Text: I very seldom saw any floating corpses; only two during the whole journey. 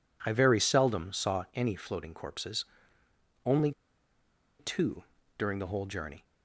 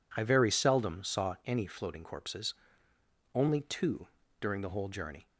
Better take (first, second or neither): second